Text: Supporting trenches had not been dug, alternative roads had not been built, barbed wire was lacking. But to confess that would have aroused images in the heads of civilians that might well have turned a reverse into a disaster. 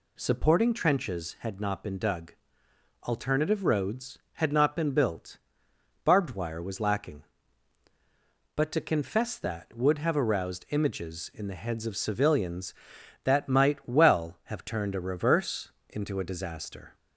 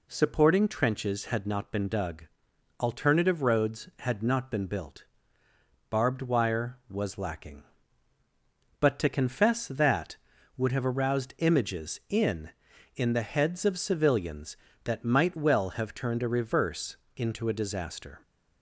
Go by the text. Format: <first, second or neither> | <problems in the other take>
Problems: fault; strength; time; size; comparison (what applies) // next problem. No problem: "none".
first | says "in" twice; at 12.9 s // pauses between "reverse" and "into"; slight; at 16.9 s; 0.22 s long; slight in the first